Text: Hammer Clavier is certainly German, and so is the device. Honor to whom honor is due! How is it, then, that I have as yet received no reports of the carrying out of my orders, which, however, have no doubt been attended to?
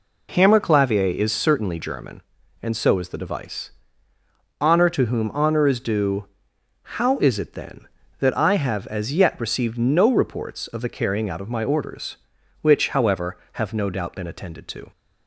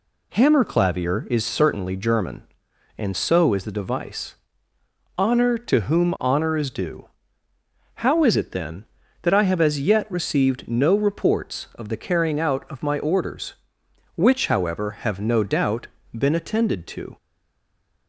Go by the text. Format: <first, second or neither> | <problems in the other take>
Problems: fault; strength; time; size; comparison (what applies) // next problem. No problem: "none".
first | pauses between "doubt" and "been"; slight; at 15.8 s; 0.28 s long // stays silent after the last word; slight; from 17.1 s on; 0.9 s long